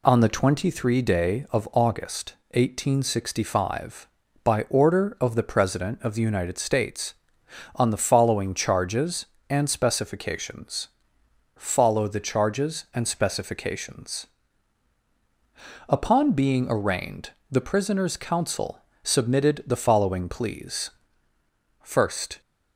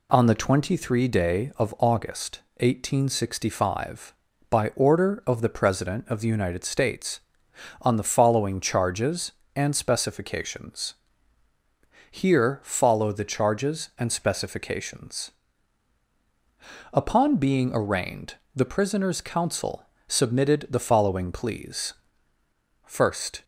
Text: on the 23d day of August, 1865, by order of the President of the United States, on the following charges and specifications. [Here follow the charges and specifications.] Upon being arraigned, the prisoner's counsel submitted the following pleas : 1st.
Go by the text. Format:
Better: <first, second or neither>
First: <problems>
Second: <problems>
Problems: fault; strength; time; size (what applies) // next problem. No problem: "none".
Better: second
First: skips "Here"; at 11.2 s // pauses between "counsel" and "submitted"; slight; at 18.8 s; 0.24 s long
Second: pauses between "counsel" and "submitted"; slight; at 19.8 s; 0.24 s long